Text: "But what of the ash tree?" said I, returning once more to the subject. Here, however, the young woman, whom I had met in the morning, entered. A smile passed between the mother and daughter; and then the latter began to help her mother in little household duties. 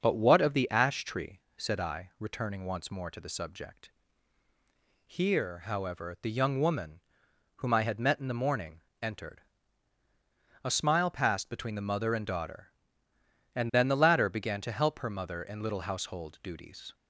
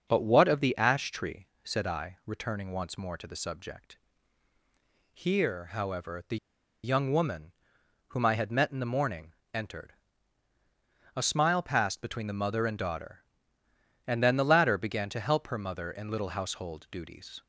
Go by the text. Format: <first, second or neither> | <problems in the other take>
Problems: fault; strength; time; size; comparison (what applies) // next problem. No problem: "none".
first | starts louder than the rest; until 1.1 s; 6.5 dB; also in the first // pauses between "the" and "young"; noticeable; at 6.3 s; 0.48 s long